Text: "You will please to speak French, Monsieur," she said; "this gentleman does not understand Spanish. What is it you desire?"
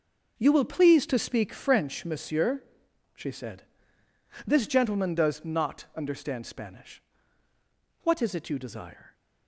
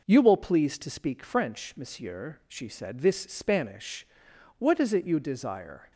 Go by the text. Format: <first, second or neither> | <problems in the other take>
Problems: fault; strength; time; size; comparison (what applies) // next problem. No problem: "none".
first | skips "gentleman does not understand"; at 3.2 s